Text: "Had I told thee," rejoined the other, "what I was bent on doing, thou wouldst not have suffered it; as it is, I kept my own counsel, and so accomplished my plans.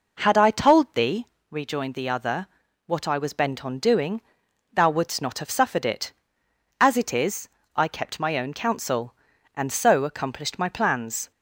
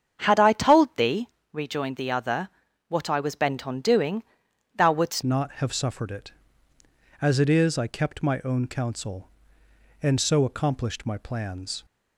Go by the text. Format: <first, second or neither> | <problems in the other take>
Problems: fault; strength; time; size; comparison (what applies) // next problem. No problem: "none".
first | starts louder than the rest; strong; until 1.2 s; 8 dB // changes voice at "not"; from 5.2 s on; 6.6 s long